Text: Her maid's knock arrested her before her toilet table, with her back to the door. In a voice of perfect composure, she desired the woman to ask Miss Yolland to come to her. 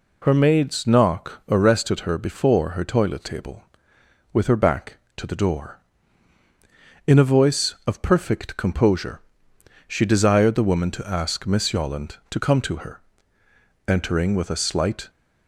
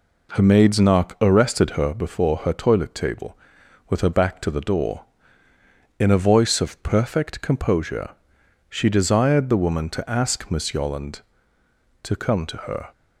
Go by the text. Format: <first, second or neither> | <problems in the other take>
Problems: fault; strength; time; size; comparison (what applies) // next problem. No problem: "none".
second | goes on to say "Entering with a slight"; noticeable; from 13.8 s on; 1.2 s long